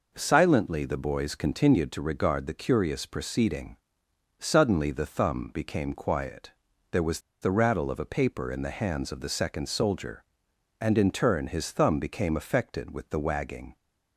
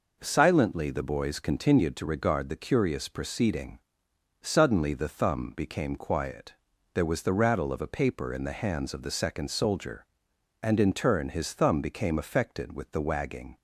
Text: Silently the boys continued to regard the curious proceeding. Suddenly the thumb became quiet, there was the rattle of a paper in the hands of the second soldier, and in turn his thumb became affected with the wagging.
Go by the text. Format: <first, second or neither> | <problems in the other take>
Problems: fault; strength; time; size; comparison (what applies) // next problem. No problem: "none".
second | pauses between "was" and "the"; slight; at 7.2 s; 0.21 s long